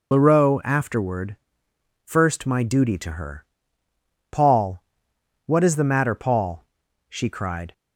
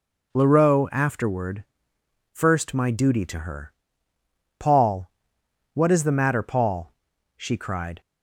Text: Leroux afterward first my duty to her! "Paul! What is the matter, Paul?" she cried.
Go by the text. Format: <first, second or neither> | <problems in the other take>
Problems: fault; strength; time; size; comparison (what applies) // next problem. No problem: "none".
second | loses the start of "Leroux"; at 0.1 s; 65 ms // pauses between "afterward" and "first"; noticeable; at 1.3 s; 0.68 s long; noticeable in the second